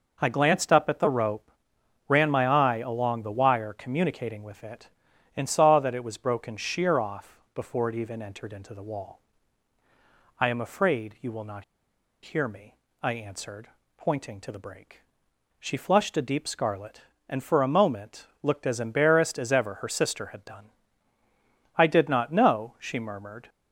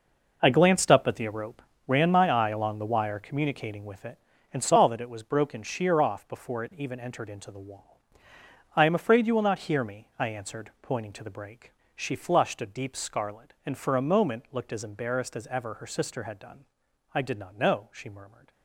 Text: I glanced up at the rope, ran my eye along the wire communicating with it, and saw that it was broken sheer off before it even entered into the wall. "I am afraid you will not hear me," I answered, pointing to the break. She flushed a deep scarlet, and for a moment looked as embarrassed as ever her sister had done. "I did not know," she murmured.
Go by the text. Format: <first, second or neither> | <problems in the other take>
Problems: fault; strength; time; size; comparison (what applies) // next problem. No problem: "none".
second | pauses between "off" and "before"; slight; at 7.3 s; 0.16 s long // pauses between "not" and "hear"; noticeable; at 11.6 s; 0.60 s long // pauses between "moment" and "looked"; slight; at 18.2 s; 0.16 s long